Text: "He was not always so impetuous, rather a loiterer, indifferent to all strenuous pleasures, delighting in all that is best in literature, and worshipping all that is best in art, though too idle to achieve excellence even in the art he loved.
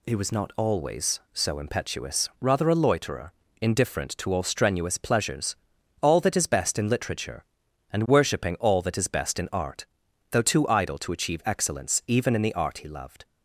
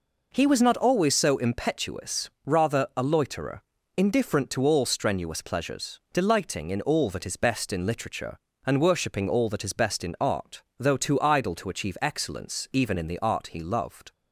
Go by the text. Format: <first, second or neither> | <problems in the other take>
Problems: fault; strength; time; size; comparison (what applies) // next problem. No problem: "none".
second | skips "delighting in"; at 5.7 s